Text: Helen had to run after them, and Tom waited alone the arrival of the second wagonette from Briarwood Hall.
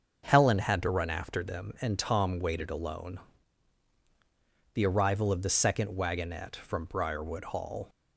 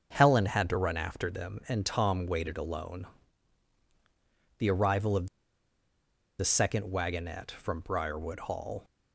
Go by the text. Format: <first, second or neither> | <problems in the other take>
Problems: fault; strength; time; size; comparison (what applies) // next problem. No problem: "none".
first | starts louder than the rest; until 1.1 s; 6.5 dB; also in the first // pauses between "alone" and "the"; strong; at 3.0 s; 1.5 s long; strong in the first // pauses between "of" and "the"; at 5.2 s; 1.1 s long